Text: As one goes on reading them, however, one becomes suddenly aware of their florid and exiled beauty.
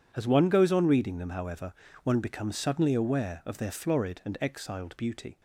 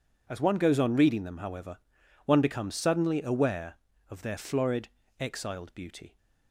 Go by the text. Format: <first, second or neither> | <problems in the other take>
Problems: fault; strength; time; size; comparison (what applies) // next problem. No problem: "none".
first | skips "and"; at 5.0 s